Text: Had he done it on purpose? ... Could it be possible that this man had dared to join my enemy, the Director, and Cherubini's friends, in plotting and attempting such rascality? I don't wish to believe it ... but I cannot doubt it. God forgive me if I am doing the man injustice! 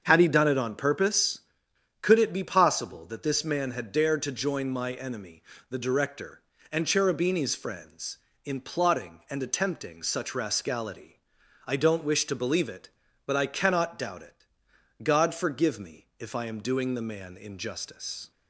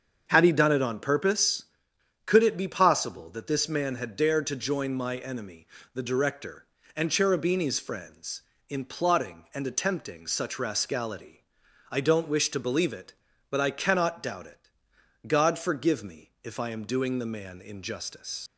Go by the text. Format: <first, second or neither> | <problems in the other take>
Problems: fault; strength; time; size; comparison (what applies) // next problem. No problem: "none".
first | starts louder than the rest; until 1.3 s; 7 dB; also in the first // leaves "injustice" unfinished; at 18.4 s; 85 ms